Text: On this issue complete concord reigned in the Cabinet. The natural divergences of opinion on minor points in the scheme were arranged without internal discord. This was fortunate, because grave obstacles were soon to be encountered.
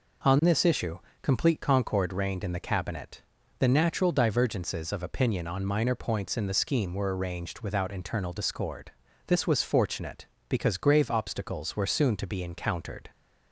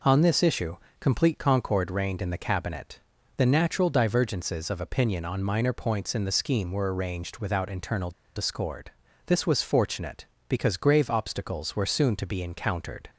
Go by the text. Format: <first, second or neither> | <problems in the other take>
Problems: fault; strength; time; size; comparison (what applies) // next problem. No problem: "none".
first | pauses between "issue" and "complete"; slight; at 0.7 s; 0.22 s long; slight in the first // pauses between "internal" and "discord"; slight; at 8.1 s; 0.24 s long